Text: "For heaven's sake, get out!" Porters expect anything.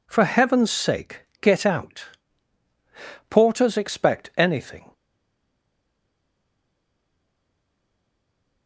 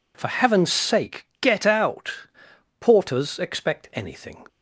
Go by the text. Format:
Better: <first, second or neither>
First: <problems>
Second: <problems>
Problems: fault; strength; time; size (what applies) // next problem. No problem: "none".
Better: second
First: stays silent after the last word; strong; from 4.9 s on; 3.7 s long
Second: none